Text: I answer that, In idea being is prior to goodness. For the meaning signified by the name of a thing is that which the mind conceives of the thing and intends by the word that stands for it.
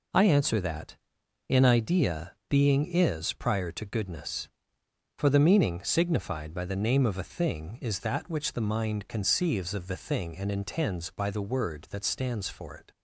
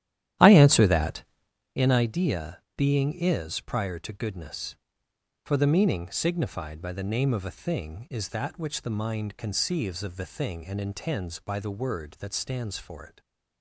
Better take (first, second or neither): first